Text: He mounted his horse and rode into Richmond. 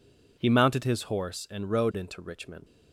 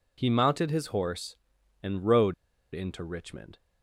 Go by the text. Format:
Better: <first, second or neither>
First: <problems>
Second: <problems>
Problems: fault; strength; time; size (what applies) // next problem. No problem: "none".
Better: first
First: none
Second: pauses between "rode" and "into"; at 2.3 s; 0.38 s long